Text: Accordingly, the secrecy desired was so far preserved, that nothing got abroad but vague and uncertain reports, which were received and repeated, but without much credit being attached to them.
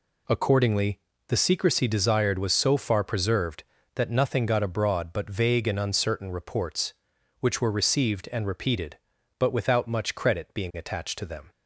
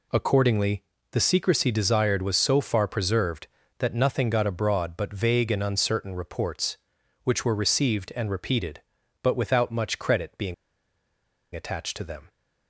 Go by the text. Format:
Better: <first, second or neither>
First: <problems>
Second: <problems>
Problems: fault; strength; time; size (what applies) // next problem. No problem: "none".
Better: first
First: none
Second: pauses between "being" and "attached"; at 10.5 s; 1.0 s long